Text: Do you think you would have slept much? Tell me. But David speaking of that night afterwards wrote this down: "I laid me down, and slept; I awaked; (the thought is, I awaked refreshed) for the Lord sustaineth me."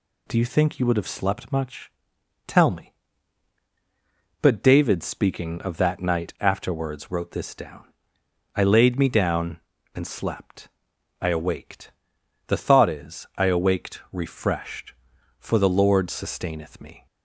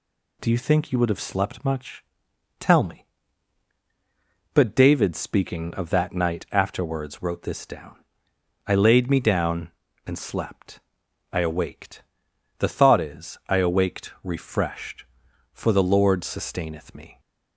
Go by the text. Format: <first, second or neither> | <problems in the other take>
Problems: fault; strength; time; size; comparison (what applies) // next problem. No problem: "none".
neither | none